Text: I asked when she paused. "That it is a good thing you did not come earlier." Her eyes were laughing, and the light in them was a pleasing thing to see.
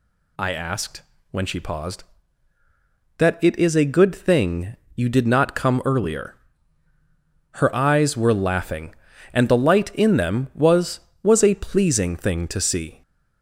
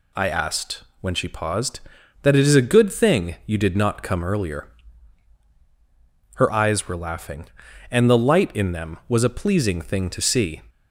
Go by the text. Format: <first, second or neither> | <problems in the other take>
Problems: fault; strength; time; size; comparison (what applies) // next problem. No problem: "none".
second | pauses between "asked" and "when"; slight; at 1.0 s; 0.28 s long; slight in the second // pauses between "thing" and "you"; slight; at 4.7 s; 0.20 s long // says "was" twice; at 11.2 s